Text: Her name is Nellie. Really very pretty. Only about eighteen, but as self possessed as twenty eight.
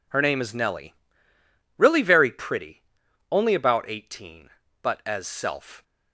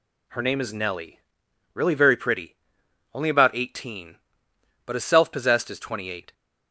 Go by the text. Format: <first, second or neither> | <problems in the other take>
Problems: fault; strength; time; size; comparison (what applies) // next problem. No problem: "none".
second | stops before "possessed as twenty eight"; at 5.8 s